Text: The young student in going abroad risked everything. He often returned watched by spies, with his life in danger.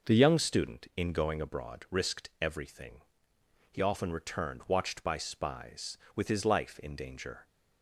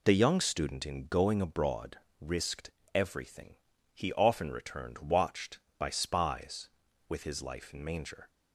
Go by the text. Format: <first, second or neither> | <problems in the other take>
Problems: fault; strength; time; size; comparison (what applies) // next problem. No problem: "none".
first | pauses between "abroad" and "risked"; slight; at 1.9 s; 0.23 s long // pauses between "risked" and "everything"; slight; at 2.6 s; 0.26 s long // says "manger" for "danger"; at 7.8 s